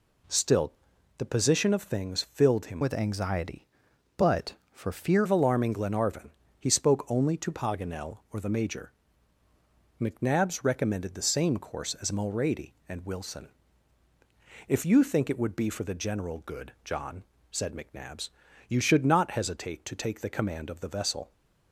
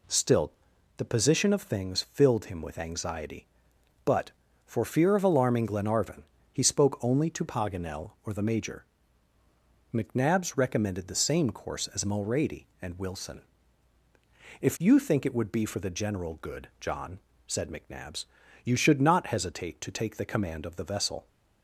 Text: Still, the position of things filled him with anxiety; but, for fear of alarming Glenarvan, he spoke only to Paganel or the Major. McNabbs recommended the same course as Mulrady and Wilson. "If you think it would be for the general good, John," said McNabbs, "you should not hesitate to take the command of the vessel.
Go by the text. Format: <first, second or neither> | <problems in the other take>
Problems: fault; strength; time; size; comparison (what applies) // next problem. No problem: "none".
second | changes voice from "with" to "fear"; from 2.8 to 5.2 s; 2.4 s long